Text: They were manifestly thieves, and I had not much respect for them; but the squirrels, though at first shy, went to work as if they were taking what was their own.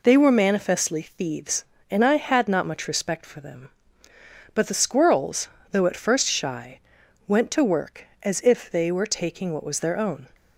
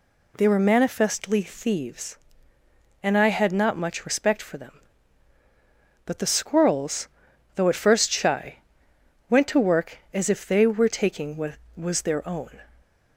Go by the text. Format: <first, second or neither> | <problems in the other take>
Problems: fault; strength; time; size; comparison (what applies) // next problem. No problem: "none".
neither | none